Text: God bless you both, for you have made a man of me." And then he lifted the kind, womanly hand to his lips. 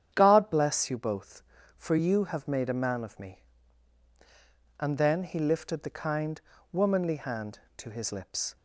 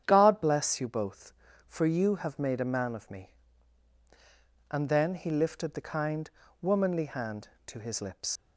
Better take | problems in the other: first | starts louder than the rest; strong; until 1.0 s; 9 dB; strong in the first // leaves "lips" unfinished; at 8.3 s; 90 ms

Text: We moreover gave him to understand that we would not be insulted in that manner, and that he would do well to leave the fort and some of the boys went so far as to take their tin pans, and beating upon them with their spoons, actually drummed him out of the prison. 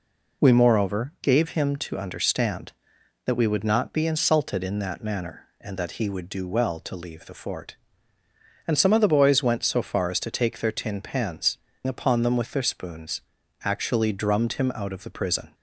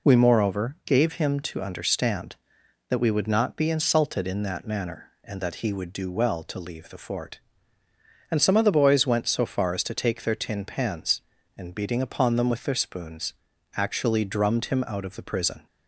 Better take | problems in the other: second | skips "and beating"; at 11.7 s

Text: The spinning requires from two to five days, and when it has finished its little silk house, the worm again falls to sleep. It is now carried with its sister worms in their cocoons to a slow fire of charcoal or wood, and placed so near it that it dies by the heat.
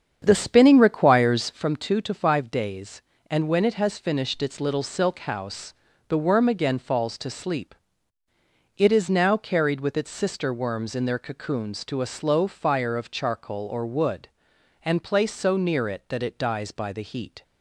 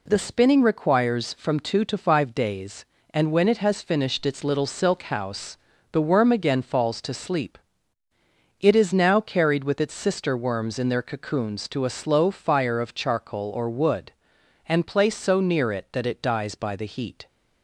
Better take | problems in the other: second | starts louder than the rest; strong; until 1.7 s; 7.5 dB

